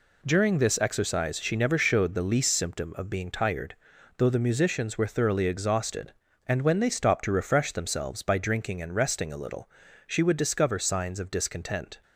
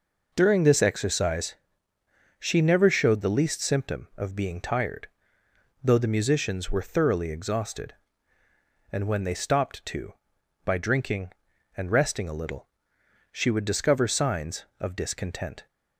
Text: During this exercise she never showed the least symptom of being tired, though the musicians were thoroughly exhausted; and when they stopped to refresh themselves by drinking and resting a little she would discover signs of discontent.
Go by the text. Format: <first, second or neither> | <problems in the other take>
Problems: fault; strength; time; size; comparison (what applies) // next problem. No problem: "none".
first | pauses between "exercise" and "she"; noticeable; at 1.5 s; 0.84 s long // skips "refresh themselves"; at 10.3 s // pauses between "little" and "she"; noticeable; at 12.6 s; 0.64 s long; also in the first